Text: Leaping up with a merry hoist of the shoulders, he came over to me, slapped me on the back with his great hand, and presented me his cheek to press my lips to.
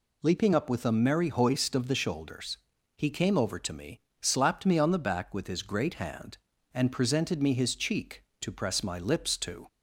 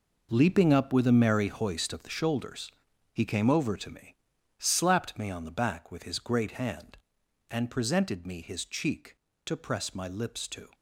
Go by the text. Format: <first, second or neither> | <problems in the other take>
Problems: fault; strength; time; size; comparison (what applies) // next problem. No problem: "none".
first | gets quieter; strong; throughout; 11.5 dB